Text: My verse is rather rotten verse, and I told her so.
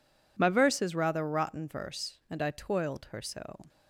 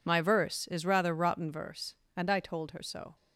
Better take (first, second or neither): second